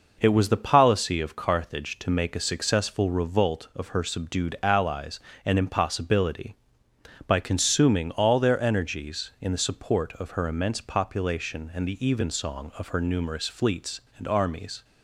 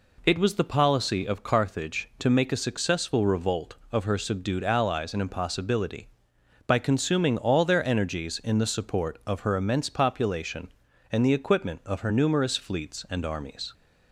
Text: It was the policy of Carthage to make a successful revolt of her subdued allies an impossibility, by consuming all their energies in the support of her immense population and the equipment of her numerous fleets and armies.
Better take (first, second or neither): second